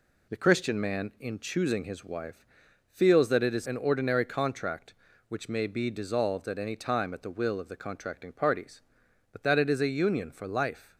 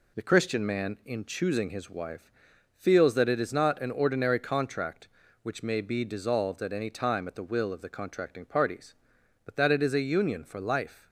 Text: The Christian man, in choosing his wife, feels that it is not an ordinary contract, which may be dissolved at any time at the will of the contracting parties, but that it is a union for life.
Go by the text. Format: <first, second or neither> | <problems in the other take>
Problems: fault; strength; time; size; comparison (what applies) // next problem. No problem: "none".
second | skips "not"; at 3.6 s